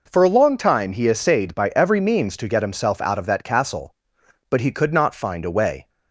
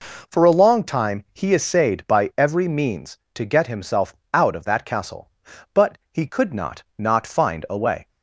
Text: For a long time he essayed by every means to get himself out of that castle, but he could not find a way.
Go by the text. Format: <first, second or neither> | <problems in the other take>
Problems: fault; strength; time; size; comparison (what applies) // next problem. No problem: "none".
first | pauses between "himself" and "out"; slight; at 4.1 s; 0.18 s long // pauses between "but" and "he"; slight; at 5.9 s; 0.16 s long // says "not" twice; at 6.9 s